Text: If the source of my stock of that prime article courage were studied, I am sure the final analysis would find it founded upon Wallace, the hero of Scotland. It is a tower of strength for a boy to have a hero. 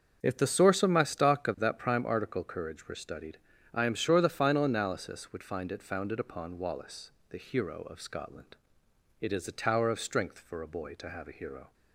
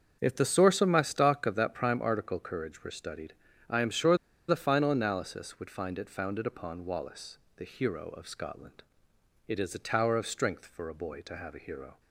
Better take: first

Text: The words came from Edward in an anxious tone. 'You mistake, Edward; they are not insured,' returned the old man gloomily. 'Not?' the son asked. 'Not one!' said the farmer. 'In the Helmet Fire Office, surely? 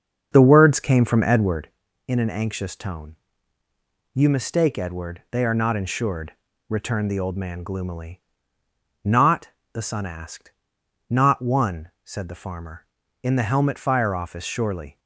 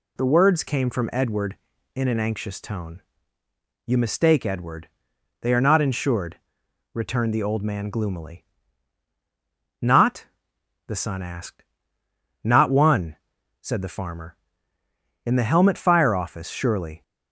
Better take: second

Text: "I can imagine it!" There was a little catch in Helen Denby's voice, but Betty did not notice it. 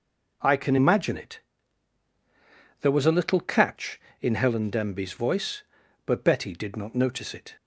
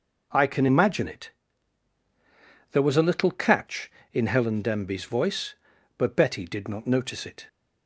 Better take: neither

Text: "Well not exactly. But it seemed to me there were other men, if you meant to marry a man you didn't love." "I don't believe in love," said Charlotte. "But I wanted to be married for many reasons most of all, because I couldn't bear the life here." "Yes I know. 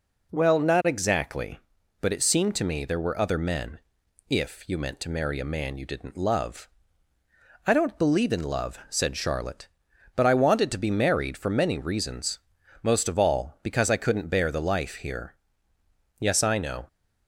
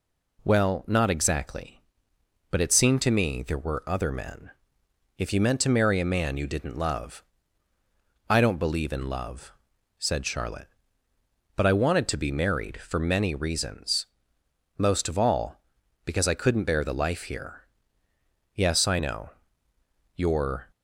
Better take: first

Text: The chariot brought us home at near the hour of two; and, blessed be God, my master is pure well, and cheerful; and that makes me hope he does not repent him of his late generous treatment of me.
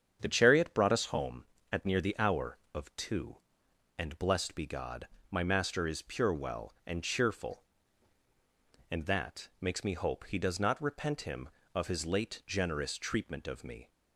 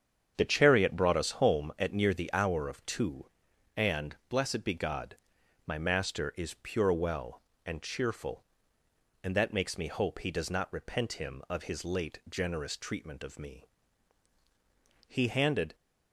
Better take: first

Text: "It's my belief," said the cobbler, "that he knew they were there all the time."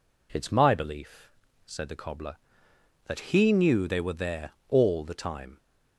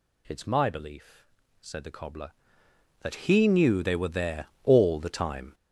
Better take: first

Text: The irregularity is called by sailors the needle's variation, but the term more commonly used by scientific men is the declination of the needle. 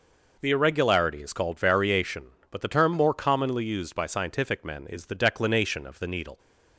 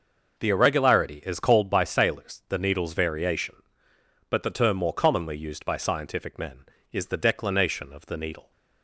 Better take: second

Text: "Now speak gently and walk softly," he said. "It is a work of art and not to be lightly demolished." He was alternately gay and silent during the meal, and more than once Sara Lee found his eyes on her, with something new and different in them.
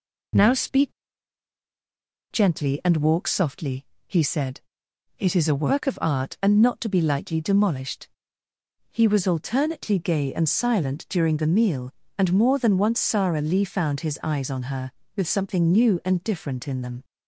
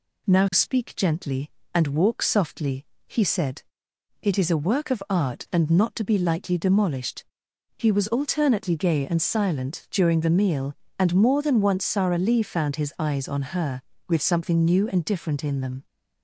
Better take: second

